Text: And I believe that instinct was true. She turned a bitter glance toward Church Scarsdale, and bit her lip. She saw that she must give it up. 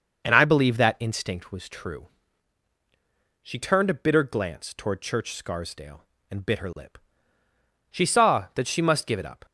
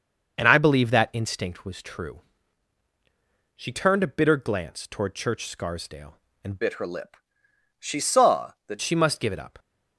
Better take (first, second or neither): first